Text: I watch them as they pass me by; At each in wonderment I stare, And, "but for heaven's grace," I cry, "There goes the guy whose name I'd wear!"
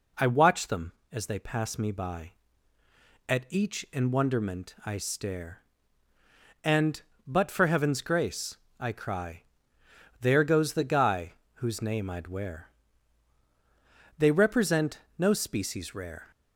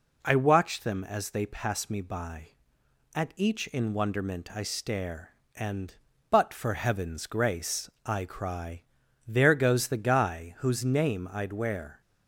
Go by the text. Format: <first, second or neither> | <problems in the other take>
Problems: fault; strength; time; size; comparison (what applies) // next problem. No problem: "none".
second | pauses between "guy" and "whose"; slight; at 11.3 s; 0.22 s long // goes on to say "They represent no species rare"; strong; from 14.1 s on; 2.1 s long